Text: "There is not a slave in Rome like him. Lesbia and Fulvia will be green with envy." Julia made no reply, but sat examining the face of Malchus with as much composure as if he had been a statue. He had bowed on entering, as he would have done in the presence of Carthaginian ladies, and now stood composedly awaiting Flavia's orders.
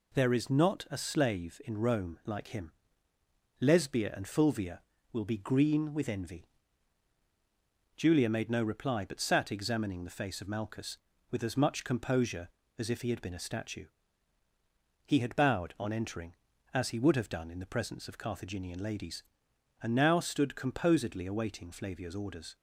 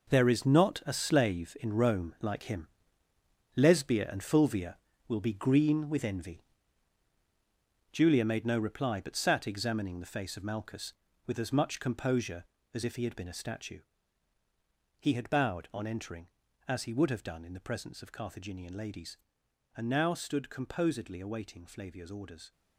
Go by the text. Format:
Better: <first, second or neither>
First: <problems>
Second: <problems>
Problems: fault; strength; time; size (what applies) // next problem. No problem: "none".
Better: first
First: none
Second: gets quieter; strong; throughout; 10 dB